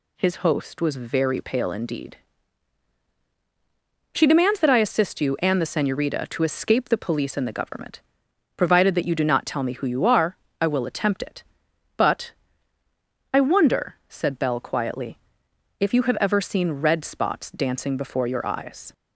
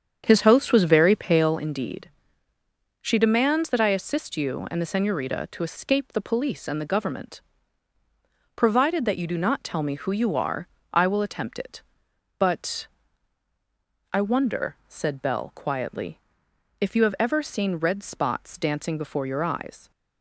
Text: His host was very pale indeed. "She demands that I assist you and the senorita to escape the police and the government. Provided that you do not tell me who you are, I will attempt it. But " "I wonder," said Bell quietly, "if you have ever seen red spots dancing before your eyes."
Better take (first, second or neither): first